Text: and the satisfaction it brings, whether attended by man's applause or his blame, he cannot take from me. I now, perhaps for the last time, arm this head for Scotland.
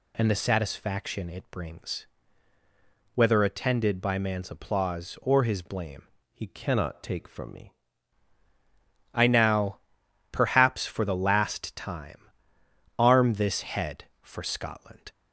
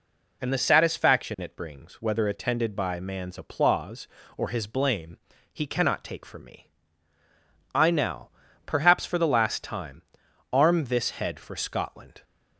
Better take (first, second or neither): second